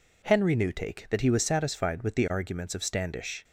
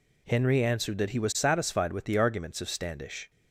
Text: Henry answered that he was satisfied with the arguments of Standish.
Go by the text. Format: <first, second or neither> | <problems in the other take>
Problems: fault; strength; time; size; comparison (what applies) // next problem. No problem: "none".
second | says "newtake" for "answered"; at 0.5 s